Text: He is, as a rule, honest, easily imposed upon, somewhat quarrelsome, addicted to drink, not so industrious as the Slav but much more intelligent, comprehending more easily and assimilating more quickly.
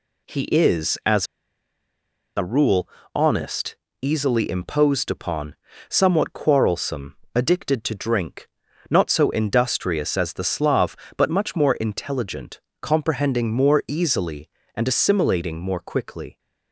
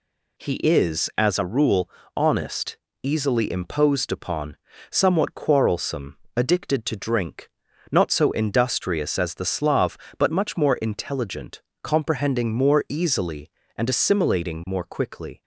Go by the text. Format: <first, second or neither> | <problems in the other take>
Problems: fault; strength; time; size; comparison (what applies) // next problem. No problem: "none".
second | pauses between "as" and "a"; at 1.2 s; 1.1 s long